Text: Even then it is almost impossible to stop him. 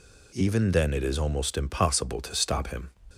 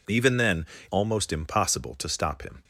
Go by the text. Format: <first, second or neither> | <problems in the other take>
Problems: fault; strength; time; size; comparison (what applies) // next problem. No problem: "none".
first | skips "it is"; at 0.7 s